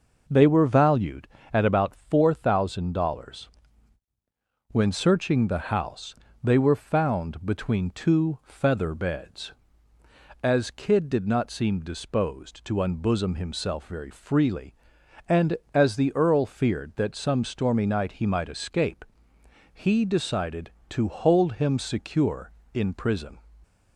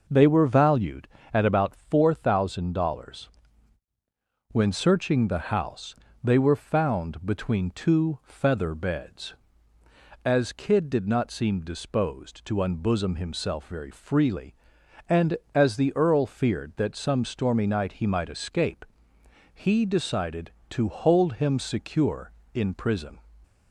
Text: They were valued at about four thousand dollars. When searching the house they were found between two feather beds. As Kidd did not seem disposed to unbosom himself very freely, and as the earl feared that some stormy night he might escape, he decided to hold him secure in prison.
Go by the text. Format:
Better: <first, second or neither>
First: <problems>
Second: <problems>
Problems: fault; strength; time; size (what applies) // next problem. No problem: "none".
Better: neither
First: pauses between "house" and "they"; slight; at 6.1 s; 0.28 s long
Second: pauses between "house" and "they"; slight; at 5.9 s; 0.28 s long